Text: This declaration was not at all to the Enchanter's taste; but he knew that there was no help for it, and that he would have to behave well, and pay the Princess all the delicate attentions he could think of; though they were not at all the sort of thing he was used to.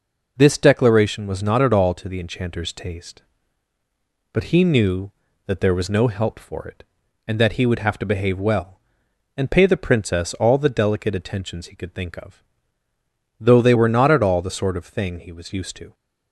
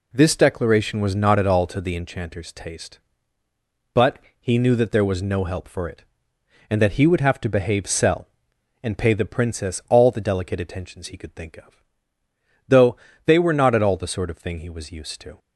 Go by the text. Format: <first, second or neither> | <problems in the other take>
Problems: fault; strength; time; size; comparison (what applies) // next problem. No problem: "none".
first | pauses between "but" and "he"; slight; at 4.1 s; 0.22 s long // says "cell" for "well"; at 7.8 s // pauses between "though" and "they"; slight; at 12.9 s; 0.30 s long